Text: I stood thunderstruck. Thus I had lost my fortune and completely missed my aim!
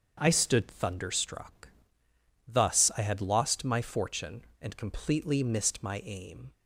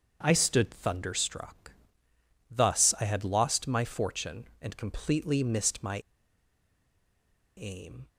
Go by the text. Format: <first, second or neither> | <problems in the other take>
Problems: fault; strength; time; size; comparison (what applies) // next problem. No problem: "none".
first | starts louder than the rest; until 1.2 s; 7 dB; also in the first // pauses between "my" and "aim"; strong; at 5.9 s; 1.6 s long